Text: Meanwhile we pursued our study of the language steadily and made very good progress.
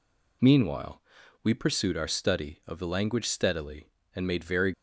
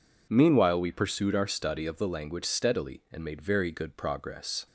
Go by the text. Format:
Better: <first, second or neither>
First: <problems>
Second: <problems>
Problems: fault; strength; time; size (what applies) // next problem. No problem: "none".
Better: second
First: pauses between "Meanwhile" and "we"; at 1.0 s; 0.42 s long // stops before "good progress"; at 4.7 s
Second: none